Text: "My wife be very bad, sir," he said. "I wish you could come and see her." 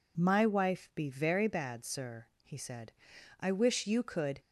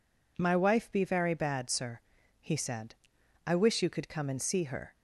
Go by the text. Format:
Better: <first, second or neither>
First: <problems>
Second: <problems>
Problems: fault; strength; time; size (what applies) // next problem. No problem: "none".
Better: second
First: stops before "come and see her"; at 4.4 s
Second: none